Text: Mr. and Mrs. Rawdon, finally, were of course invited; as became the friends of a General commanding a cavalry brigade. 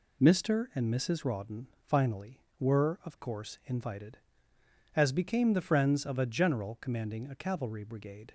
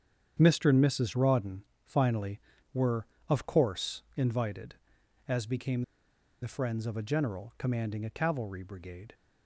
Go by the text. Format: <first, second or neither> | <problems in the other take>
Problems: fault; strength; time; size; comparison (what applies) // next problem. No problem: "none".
first | starts louder than the rest; strong; until 1.4 s; 8 dB // pauses between "became" and "the"; noticeable; at 5.8 s; 0.60 s long